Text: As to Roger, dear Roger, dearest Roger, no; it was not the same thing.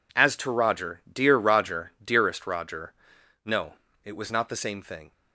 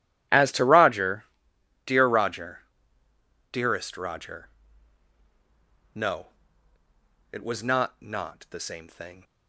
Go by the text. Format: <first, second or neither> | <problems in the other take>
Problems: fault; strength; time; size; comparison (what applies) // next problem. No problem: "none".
first | says "not" twice; at 8.0 s